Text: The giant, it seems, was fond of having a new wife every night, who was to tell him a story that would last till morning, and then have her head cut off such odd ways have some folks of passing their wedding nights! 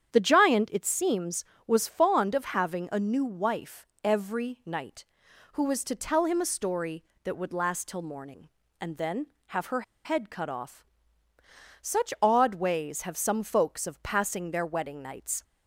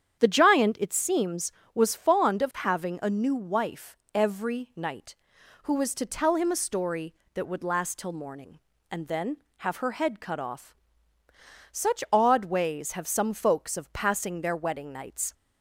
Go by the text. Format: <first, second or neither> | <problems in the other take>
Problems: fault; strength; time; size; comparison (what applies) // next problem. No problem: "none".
second | starts louder than the rest; strong; until 1.1 s; 8.5 dB; strong in the second // pauses between "wife" and "every"; slight; at 3.8 s; 0.16 s long; slight in the second // pauses between "her" and "head"; slight; at 9.8 s; 0.22 s long // pauses between "off" and "such"; noticeable; at 10.8 s; 0.98 s long; noticeable in the second